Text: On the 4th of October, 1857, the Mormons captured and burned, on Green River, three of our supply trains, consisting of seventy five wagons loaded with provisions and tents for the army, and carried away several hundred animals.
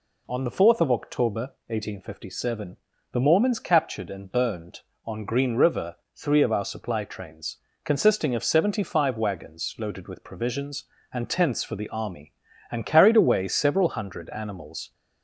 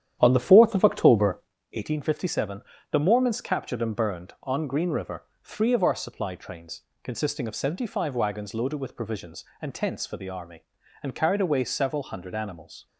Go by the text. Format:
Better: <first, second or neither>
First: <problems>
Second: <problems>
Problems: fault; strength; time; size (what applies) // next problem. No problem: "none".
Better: first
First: none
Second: starts louder than the rest; strong; until 1.6 s; 10 dB